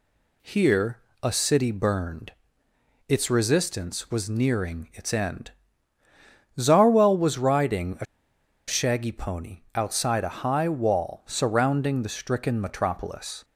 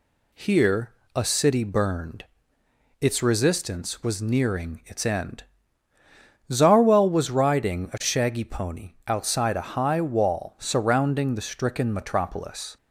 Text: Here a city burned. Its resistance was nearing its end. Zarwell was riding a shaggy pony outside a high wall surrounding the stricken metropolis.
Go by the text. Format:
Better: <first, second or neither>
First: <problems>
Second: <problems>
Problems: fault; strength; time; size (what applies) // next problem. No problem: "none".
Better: second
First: pauses between "Here" and "a"; slight; at 0.9 s; 0.24 s long // pauses between "a" and "shaggy"; noticeable; at 8.0 s; 0.63 s long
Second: pauses between "Here" and "a"; slight; at 0.9 s; 0.24 s long